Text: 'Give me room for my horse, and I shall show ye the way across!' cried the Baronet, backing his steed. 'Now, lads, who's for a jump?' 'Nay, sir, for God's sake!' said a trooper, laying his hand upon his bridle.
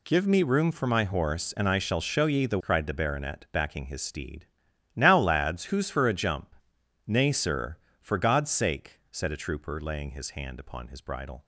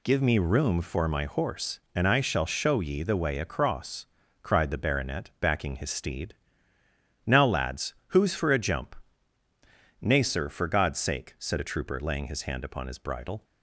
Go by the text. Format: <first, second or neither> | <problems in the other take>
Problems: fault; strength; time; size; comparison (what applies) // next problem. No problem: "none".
second | skips "way across"; at 2.5 s